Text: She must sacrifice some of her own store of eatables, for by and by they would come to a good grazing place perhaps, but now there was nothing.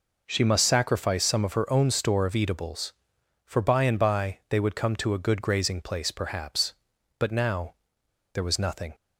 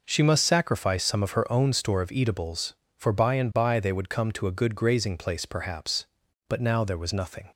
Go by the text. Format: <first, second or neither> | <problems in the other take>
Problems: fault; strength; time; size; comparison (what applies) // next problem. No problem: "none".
second | pauses between "now" and "there"; noticeable; at 7.7 s; 0.58 s long